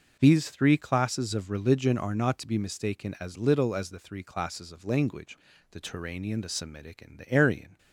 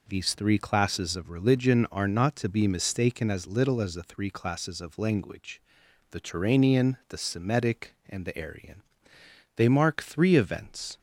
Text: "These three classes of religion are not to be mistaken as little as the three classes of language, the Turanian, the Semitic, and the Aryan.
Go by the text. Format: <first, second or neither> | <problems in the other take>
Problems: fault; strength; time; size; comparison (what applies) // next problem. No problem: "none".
first | goes on to say "They mark three events"; from 9.5 s on; 1.4 s long